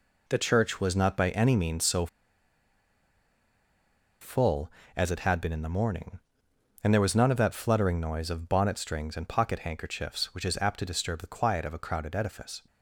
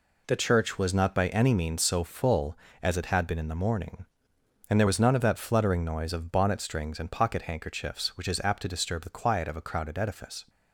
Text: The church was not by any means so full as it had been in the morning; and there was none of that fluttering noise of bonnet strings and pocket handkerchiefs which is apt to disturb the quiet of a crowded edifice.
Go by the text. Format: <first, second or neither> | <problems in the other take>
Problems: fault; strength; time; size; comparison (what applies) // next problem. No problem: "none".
second | pauses between "so" and "full"; strong; at 2.0 s; 2.1 s long